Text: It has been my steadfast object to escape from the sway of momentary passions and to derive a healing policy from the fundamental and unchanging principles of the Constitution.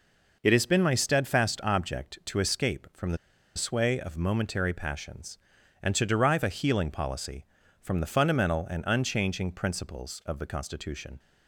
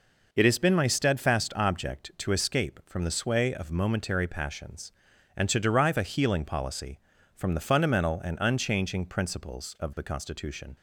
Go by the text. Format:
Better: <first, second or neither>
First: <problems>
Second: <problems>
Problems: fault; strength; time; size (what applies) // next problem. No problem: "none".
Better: second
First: pauses between "the" and "sway"; at 3.1 s; 0.39 s long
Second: none